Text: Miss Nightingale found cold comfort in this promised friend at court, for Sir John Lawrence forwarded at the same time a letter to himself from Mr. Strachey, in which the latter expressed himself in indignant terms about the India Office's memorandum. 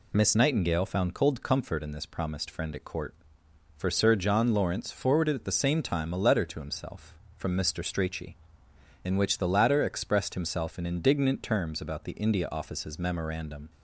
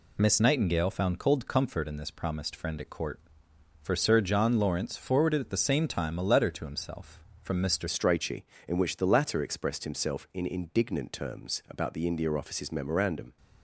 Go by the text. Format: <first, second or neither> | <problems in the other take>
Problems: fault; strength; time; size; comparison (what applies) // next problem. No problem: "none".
first | changes voice at "Strachey"; from 7.8 s on; 5.5 s long